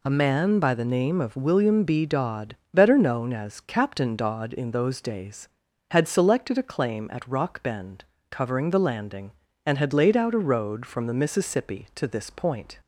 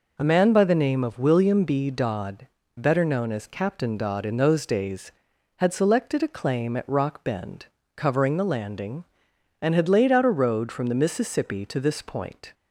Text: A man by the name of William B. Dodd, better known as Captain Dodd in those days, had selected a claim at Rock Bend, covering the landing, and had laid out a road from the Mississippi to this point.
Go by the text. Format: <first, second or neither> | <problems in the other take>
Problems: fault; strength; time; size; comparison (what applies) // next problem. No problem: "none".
neither | none